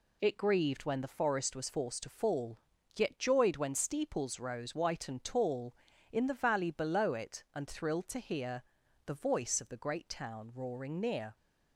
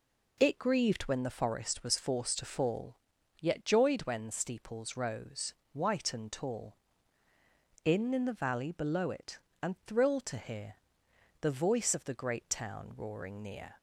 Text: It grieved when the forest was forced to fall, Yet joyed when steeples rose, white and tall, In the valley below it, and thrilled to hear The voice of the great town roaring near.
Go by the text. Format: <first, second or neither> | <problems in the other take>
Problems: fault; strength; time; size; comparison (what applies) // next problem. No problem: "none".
first | says "In" twice; at 8.1 s // pauses between "hear" and "The"; noticeable; at 10.7 s; 0.66 s long; also in the first